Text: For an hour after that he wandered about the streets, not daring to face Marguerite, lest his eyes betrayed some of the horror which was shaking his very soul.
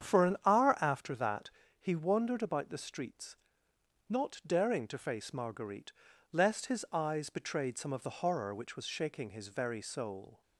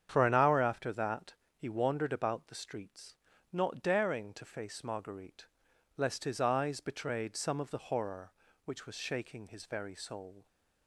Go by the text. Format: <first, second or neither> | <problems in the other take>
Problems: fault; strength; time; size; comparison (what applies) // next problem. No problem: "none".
neither | starts louder than the rest; strong; the same in both // pauses between "that" and "he"; slight; the same in both